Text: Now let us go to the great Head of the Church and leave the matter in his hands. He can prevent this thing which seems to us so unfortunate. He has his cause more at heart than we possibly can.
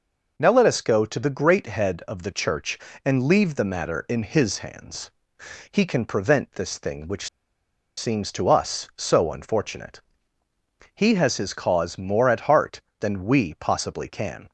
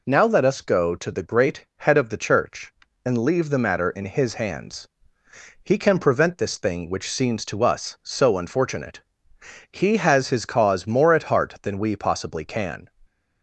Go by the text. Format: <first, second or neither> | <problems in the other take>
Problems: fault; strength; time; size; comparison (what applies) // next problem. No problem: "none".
second | pauses between "which" and "seems"; noticeable; at 7.2 s; 0.68 s long